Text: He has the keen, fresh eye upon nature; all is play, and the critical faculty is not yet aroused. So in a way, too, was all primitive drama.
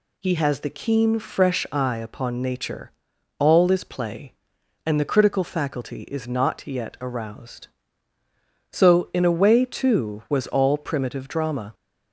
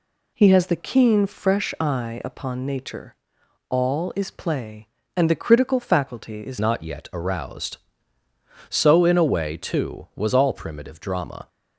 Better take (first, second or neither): first